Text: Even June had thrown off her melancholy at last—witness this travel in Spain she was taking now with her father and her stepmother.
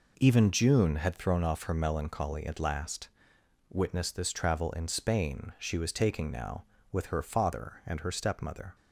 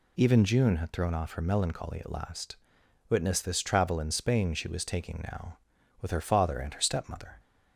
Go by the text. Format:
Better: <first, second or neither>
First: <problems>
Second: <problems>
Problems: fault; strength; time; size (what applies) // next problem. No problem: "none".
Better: neither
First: none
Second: none